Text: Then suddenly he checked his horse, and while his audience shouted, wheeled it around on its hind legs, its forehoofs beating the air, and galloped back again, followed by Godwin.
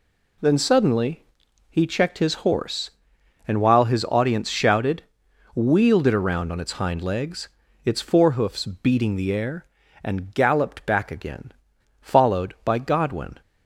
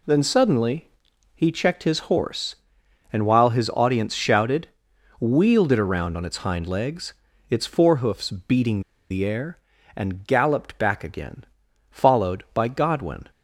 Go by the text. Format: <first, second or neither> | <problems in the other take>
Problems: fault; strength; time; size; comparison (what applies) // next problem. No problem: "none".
first | pauses between "suddenly" and "he"; noticeable; at 0.8 s; 0.46 s long; noticeable in the first // pauses between "forehoofs" and "beating"; slight; at 8.3 s; 0.16 s long; slight in the first // pauses between "beating" and "the"; slight; at 8.8 s; 0.29 s long